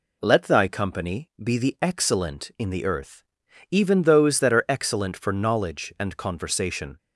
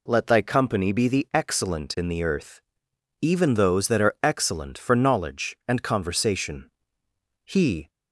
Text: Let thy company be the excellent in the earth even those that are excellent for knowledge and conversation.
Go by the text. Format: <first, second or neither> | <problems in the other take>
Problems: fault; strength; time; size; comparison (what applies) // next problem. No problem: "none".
first | pauses between "earth" and "even"; noticeable; at 2.6 s; 0.60 s long; noticeable in the first // goes on to say "He"; slight; from 7.4 s on; 0.44 s long